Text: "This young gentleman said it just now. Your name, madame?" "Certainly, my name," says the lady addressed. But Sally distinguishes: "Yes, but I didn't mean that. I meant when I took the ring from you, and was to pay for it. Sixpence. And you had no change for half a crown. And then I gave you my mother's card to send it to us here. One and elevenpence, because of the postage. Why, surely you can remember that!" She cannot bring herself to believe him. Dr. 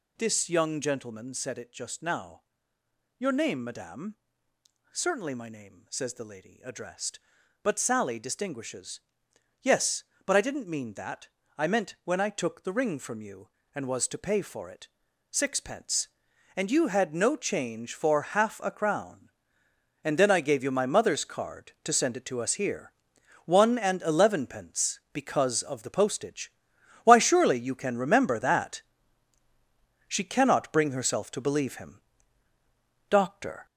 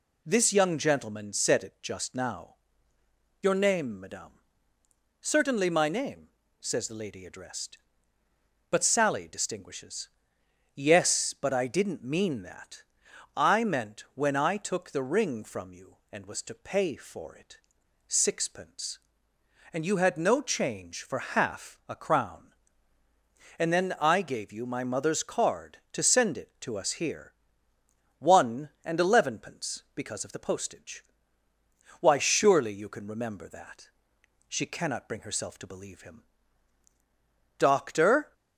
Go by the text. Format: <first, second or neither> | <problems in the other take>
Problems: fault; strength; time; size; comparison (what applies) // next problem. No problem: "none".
second | gets louder; noticeable; throughout; 5.5 dB